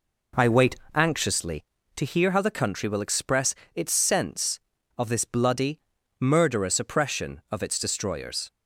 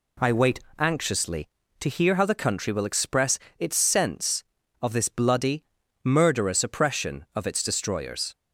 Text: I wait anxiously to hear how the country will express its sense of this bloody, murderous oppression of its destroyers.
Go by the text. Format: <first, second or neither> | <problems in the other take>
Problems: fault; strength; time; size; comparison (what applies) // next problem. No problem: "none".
second | starts louder than the rest; noticeable; until 1.4 s; 4 dB // pauses between "wait" and "anxiously"; slight; at 0.7 s; 0.20 s long; slight in the second // pauses between "express" and "its"; slight; at 3.5 s; 0.20 s long; slight in the second